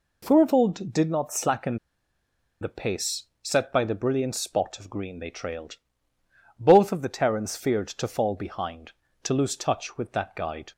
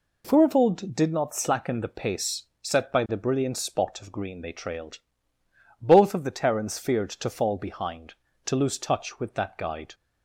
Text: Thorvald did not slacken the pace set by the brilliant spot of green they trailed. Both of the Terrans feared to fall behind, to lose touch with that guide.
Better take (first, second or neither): second